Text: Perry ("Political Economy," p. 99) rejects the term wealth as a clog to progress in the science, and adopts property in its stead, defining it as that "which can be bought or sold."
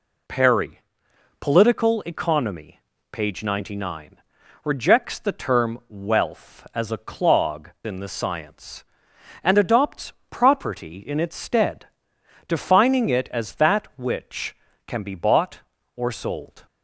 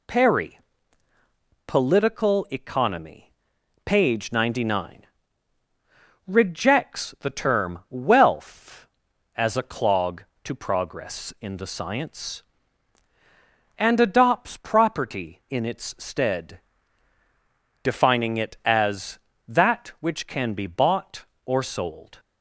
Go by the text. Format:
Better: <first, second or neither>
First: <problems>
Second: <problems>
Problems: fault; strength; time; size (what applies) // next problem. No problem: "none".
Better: second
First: skips "to progress"; at 7.7 s // pauses between "adopts" and "property"; slight; at 10.1 s; 0.16 s long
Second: none